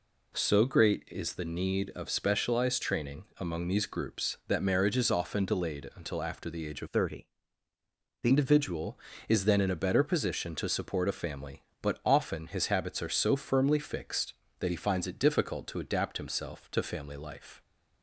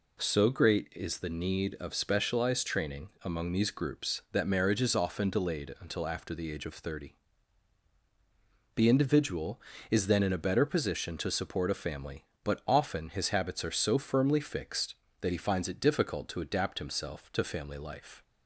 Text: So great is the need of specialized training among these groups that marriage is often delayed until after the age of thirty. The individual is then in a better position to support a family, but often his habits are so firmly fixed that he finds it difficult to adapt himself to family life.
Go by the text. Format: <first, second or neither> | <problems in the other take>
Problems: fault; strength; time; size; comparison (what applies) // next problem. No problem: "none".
second | changes voice from "thirty" to "The"; from 6.8 to 8.3 s; 1.5 s long